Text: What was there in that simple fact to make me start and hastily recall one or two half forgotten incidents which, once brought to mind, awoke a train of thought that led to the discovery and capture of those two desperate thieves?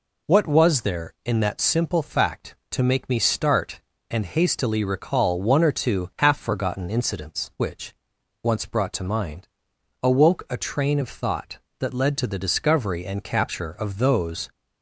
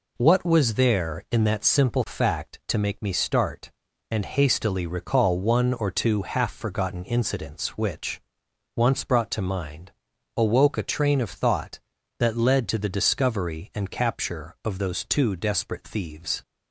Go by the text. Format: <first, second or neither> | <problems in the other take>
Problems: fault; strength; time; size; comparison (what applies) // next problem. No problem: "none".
second | stops before "two desperate thieves"; at 14.5 s